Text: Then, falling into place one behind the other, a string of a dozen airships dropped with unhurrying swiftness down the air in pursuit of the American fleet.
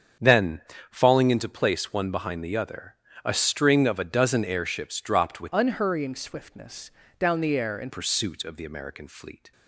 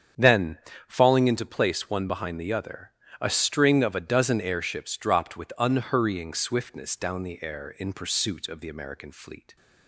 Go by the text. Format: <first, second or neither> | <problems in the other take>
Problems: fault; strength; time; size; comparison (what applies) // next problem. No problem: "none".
second | starts louder than the rest; strong; until 1.4 s; 7.5 dB; strong in the second // changes voice from "unhurrying" to "in"; from 5.5 to 7.9 s; 2.4 s long // pauses between "swiftness" and "down"; slight; at 6.9 s; 0.28 s long